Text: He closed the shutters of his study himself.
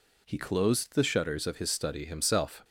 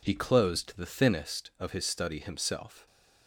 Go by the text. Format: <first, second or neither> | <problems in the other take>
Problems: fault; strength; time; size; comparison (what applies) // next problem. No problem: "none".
first | says "thinnest" for "shutters"; at 0.8 s